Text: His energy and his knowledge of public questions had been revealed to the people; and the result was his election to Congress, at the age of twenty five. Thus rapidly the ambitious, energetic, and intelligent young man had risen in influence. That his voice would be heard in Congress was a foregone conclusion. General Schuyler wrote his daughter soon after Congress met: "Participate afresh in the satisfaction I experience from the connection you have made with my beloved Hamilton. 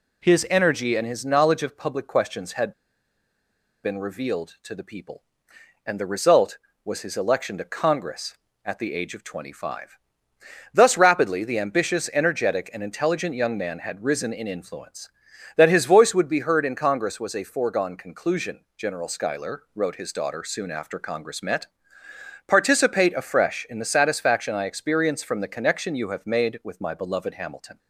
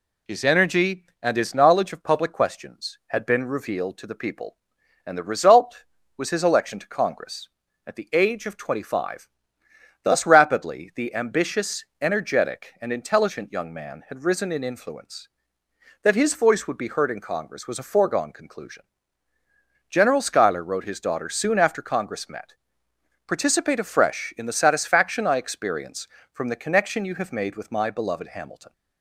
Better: second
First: pauses between "had" and "been"; at 2.7 s; 1.1 s long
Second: none

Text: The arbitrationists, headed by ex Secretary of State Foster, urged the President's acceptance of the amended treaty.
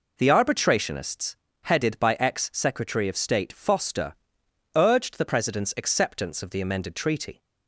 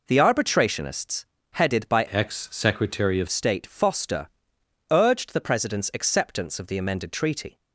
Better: first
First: none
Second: changes voice from "ex" to "of"; from 2.0 to 3.2 s; 1.2 s long

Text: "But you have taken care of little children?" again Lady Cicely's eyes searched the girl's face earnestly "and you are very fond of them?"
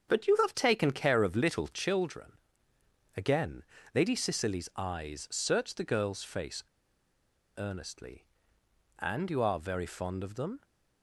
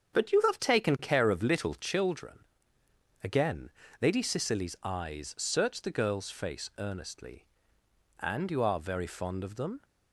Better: second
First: starts louder than the rest; strong; until 1.1 s; 7.5 dB // pauses between "again" and "Lady"; slight; at 3.6 s; 0.32 s long // pauses between "face" and "earnestly"; noticeable; at 6.6 s; 0.94 s long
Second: starts louder than the rest; strong; until 1.2 s; 7.5 dB // pauses between "again" and "Lady"; slight; at 3.6 s; 0.32 s long

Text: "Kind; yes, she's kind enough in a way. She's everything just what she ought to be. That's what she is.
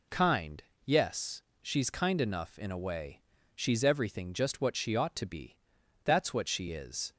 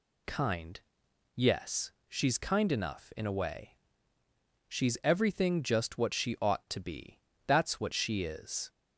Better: neither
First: none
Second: none

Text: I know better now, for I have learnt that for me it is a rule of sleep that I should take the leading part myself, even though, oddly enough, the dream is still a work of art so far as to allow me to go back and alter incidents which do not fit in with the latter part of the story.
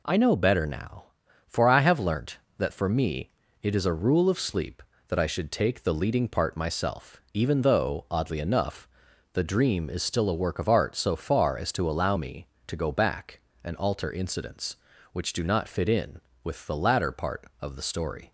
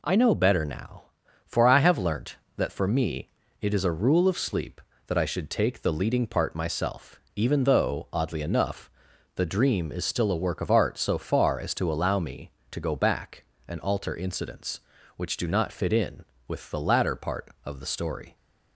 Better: neither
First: pauses between "me" and "it"; slight; at 3.3 s; 0.30 s long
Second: pauses between "me" and "it"; slight; at 3.2 s; 0.30 s long

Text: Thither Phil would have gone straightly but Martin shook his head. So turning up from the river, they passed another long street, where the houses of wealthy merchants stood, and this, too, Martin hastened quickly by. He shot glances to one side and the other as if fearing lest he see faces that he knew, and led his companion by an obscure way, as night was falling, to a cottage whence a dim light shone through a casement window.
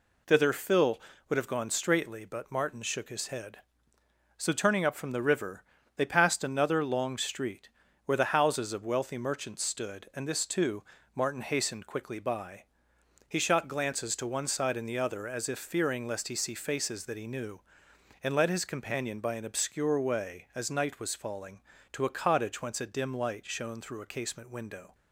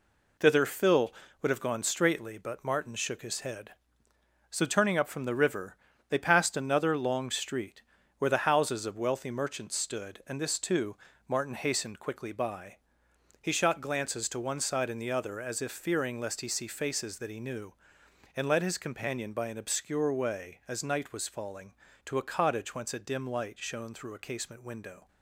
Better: first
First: none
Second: gets quieter; throughout; 6.5 dB

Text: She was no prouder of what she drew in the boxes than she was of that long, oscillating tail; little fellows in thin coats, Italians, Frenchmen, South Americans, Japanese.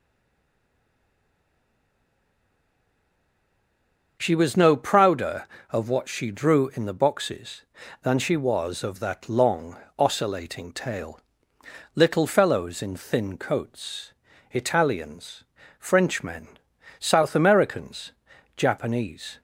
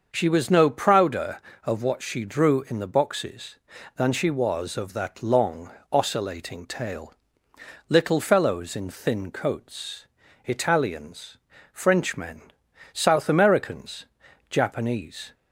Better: second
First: stays silent before the first word; strong; until 4.1 s; 4.1 s long // starts louder than the rest; until 5.2 s; 6.5 dB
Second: starts louder than the rest; until 1.1 s; 6.5 dB

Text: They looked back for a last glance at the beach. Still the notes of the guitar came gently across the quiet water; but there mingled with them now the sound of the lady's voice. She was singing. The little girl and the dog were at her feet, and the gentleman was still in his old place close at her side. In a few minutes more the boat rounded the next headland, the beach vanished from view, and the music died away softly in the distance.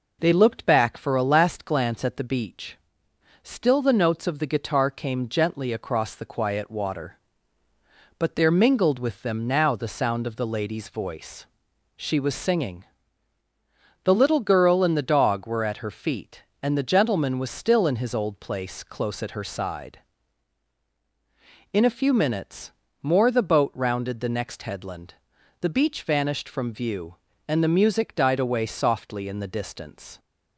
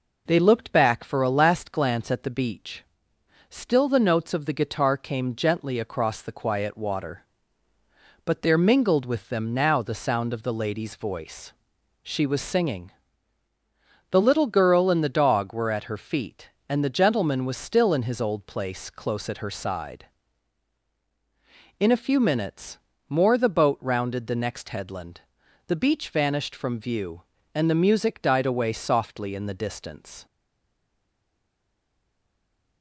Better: first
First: pauses between "minutes" and "more"; slight; at 22.7 s; 0.28 s long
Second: pauses between "minutes" and "more"; slight; at 22.7 s; 0.28 s long // stays silent after the last word; strong; from 30.2 s on; 2.6 s long

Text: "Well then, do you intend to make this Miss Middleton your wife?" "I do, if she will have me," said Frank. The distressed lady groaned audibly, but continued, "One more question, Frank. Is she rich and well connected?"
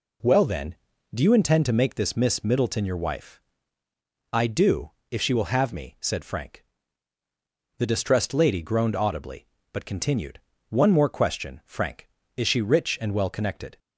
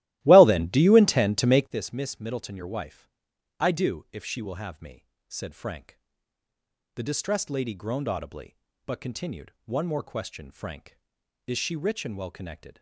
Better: first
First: none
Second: starts louder than the rest; strong; until 1.8 s; 16 dB

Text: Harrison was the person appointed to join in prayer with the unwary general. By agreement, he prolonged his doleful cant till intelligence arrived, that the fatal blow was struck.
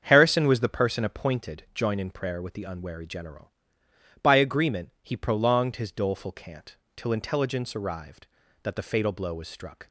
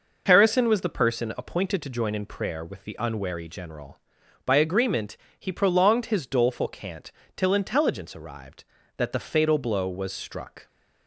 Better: second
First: starts louder than the rest; strong; until 1.0 s; 7.5 dB // skips "to"; at 1.6 s // pauses between "cant" and "till"; slight; at 6.7 s; 0.22 s long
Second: pauses between "cant" and "till"; slight; at 7.1 s; 0.24 s long

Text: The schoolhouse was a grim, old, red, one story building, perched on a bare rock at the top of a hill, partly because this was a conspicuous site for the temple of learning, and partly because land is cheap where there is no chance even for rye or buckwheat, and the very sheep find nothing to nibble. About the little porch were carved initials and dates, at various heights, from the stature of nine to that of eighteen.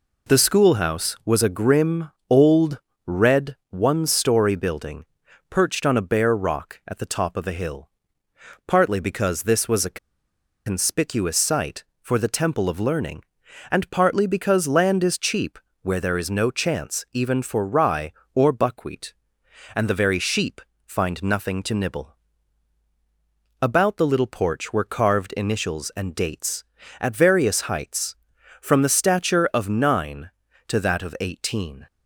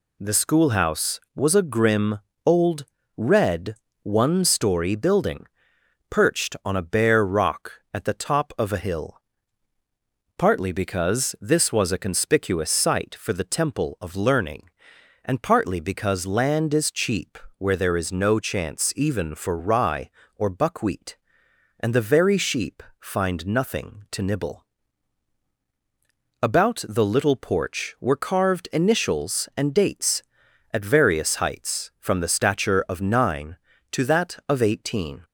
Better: second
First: pauses between "a" and "conspicuous"; noticeable; at 9.9 s; 0.67 s long // pauses between "cheap" and "where"; slight; at 15.5 s; 0.24 s long // pauses between "sheep" and "find"; slight; at 20.6 s; 0.26 s long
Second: pauses between "cheap" and "where"; slight; at 17.3 s; 0.22 s long // pauses between "sheep" and "find"; slight; at 22.8 s; 0.16 s long

